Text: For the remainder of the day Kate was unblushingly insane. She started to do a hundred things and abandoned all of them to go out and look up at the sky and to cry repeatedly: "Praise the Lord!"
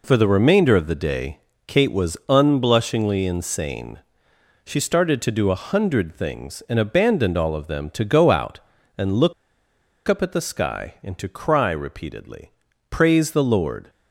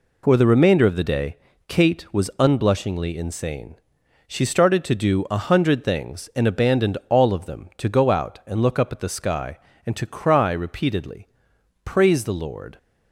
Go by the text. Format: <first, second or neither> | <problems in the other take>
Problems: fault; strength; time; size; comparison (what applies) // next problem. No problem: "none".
second | pauses between "day" and "Kate"; slight; at 1.3 s; 0.26 s long; slight in the second // pauses between "look" and "up"; noticeable; at 9.3 s; 0.74 s long